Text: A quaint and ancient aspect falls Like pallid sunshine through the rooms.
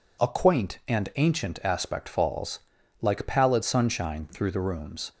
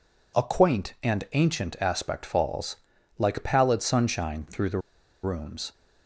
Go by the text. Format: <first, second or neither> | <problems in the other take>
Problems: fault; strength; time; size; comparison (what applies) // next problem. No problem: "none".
first | pauses between "falls" and "Like"; at 2.7 s; 0.44 s long; also in the first // pauses between "the" and "rooms"; at 4.8 s; 0.43 s long